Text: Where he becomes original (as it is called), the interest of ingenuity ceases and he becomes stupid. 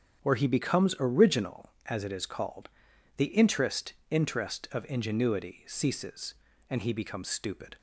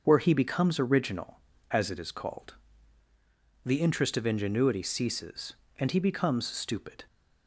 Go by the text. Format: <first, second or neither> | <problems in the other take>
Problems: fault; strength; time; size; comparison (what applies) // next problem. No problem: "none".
second | starts louder than the rest; strong; until 1.2 s; 8.5 dB; also in the second // says "interest" twice; at 4.0 s